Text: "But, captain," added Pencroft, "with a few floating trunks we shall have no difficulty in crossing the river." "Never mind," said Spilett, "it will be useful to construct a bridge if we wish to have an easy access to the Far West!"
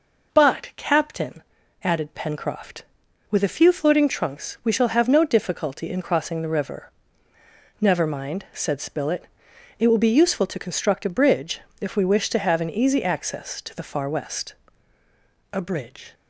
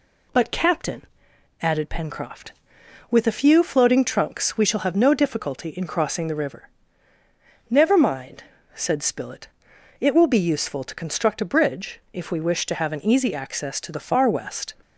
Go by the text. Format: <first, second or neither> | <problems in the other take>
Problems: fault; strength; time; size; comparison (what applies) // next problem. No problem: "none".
second | pauses between "bridge" and "if"; slight; at 11.6 s; 0.20 s long // goes on to say "A bridge"; noticeable; from 15.5 s on; 0.62 s long